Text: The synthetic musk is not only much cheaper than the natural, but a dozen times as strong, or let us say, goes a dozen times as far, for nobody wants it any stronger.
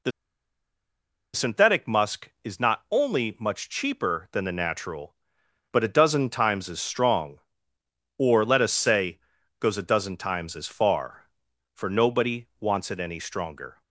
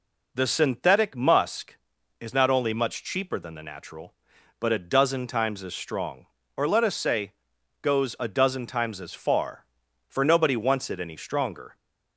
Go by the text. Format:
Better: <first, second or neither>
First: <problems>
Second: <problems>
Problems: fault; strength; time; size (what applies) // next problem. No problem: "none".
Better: second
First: pauses between "The" and "synthetic"; at 0.1 s; 1.2 s long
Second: none